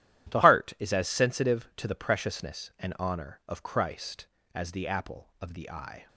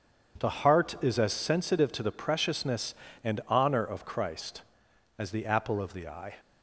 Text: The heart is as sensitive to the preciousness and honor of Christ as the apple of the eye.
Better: second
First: starts louder than the rest; strong; until 1.3 s; 12.5 dB // changes voice at "heart"; from 0.4 s on; 5.6 s long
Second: none

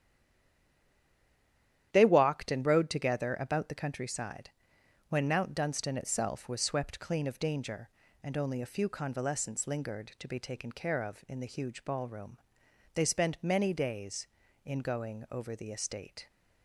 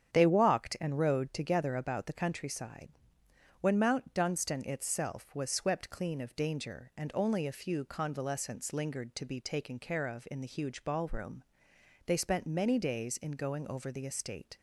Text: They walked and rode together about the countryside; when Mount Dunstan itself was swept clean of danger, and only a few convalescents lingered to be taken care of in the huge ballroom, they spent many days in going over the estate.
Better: second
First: stays silent before the first word; noticeable; until 1.9 s; 1.9 s long // starts louder than the rest; strong; until 2.9 s; 10.5 dB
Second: starts louder than the rest; strong; until 1.1 s; 9 dB

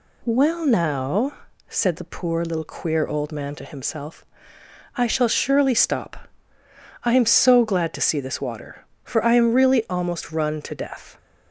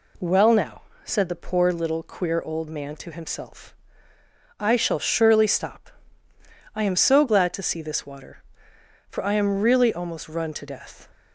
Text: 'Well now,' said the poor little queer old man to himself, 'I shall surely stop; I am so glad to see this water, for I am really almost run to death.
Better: neither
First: none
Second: none

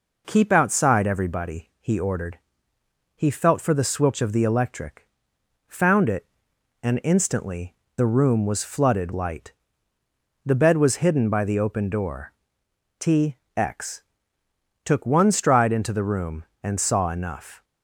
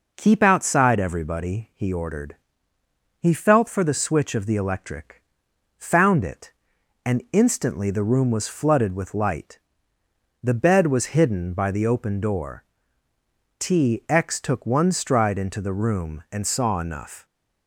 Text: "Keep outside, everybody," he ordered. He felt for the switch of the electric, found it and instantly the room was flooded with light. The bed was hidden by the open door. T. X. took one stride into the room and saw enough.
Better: second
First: pauses between "instantly" and "the"; slight; at 7.7 s; 0.20 s long // skips "with"; at 9.1 s // pauses between "T" and "X"; slight; at 13.3 s; 0.20 s long // pauses between "X" and "took"; noticeable; at 14.0 s; 0.80 s long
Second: none

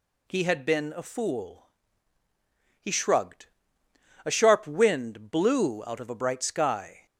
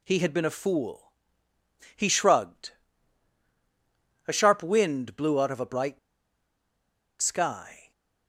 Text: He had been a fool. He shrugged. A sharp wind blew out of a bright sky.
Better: first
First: none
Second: pauses between "bright" and "sky"; at 5.9 s; 1.2 s long

